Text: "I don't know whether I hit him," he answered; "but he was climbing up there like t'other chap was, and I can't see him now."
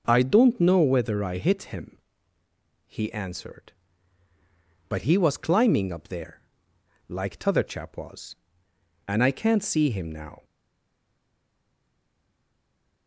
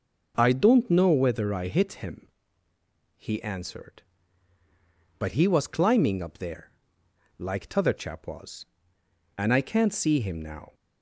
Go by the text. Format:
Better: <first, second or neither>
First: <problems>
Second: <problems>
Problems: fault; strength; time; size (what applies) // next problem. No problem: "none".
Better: second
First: pauses between "there" and "like"; noticeable; at 6.4 s; 0.66 s long // stays silent after the last word; strong; from 10.4 s on; 2.6 s long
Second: pauses between "there" and "like"; noticeable; at 6.7 s; 0.66 s long